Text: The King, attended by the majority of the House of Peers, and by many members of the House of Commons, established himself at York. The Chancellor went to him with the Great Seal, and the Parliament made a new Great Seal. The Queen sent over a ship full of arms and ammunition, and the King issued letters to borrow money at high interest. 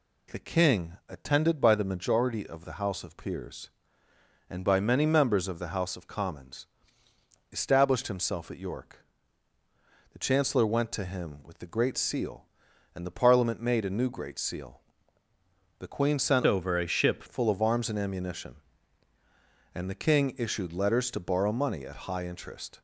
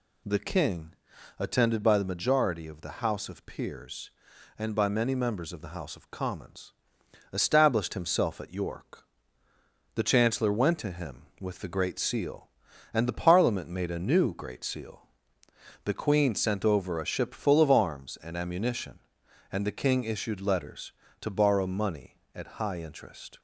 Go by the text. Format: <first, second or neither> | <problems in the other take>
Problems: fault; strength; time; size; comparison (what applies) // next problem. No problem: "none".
second | changes voice from "over" to "ship"; from 16.4 to 17.2 s; 0.8 s long